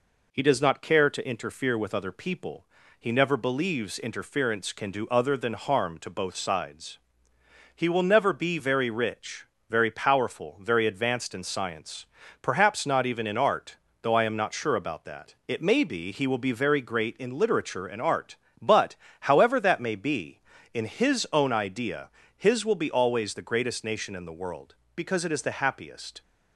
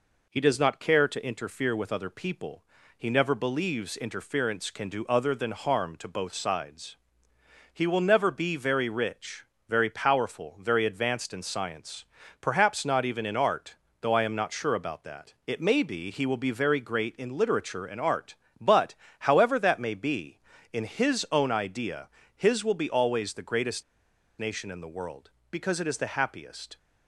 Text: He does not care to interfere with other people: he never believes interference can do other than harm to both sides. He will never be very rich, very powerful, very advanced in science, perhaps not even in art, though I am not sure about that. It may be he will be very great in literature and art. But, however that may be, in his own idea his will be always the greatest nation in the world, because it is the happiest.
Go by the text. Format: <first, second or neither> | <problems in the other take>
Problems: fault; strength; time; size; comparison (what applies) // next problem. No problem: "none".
first | pauses between "idea" and "his"; slight; at 22.0 s; 0.28 s long; slight in the first // pauses between "greatest" and "nation"; noticeable; at 23.8 s; 0.55 s long